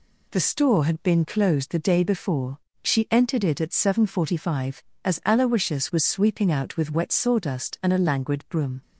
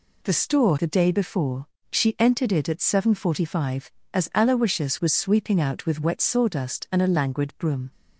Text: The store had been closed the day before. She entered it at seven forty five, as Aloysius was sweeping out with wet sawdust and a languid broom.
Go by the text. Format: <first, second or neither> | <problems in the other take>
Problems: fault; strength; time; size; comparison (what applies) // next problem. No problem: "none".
first | skips "had been closed"; at 0.7 s